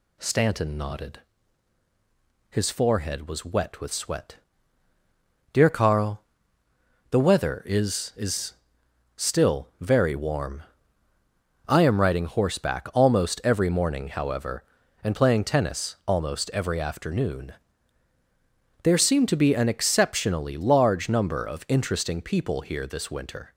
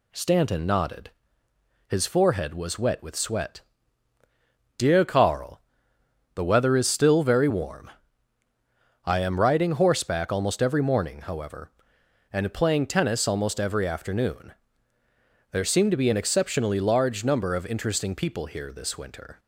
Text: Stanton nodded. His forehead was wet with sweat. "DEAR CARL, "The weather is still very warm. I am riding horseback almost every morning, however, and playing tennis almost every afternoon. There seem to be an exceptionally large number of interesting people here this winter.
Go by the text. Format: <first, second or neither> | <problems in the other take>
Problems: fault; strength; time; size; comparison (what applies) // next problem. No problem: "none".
second | says "is" twice; at 8.1 s